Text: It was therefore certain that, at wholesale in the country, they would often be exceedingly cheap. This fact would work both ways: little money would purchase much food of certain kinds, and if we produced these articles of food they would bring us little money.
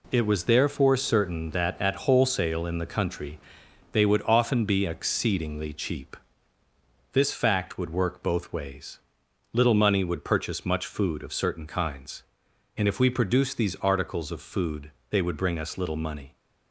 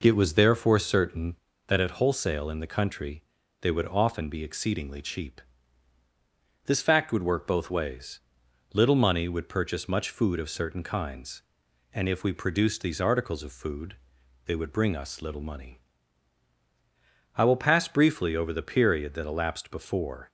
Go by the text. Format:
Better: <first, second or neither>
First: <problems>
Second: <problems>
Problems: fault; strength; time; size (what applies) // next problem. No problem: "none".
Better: first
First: pauses between "food" and "they"; slight; at 14.9 s; 0.18 s long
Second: pauses between "food" and "they"; noticeable; at 13.9 s; 0.48 s long // goes on to say "I will pass briefly over the period that elapsed before"; strong; from 17.3 s on; 2.9 s long